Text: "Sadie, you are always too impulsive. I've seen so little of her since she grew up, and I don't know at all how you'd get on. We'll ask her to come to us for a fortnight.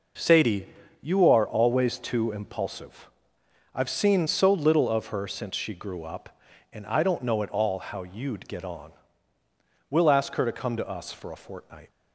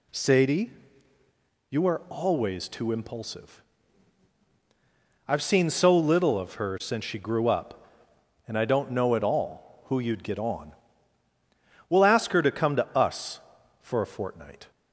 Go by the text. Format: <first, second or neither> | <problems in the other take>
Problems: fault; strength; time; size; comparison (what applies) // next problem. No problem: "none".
first | says "who" for "how"; at 9.8 s